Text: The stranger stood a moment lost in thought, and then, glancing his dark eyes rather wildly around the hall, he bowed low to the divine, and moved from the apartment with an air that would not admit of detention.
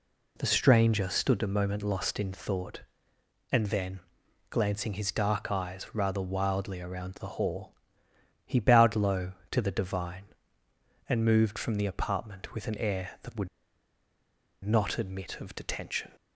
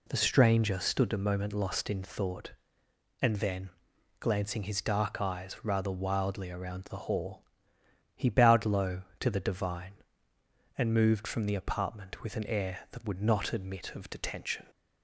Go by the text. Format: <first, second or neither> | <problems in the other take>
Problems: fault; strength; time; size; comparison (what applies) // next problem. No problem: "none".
second | pauses between "would" and "not"; at 13.4 s; 1.1 s long